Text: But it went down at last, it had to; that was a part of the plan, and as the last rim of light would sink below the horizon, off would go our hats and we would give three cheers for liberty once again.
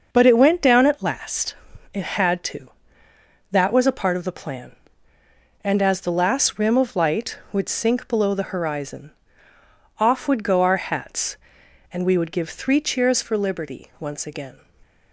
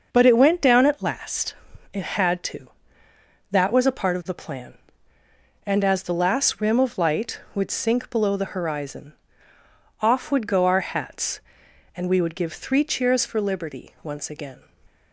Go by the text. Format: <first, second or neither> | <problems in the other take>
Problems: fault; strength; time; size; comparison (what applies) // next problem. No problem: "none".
neither | starts louder than the rest; the same in both